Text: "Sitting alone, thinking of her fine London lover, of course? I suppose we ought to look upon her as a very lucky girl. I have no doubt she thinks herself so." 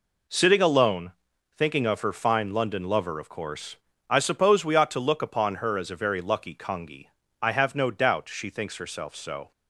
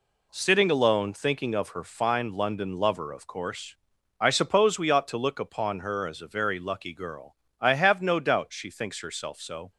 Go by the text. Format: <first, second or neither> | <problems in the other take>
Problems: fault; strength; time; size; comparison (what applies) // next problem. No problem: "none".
second | says "congi" for "girl"; at 6.5 s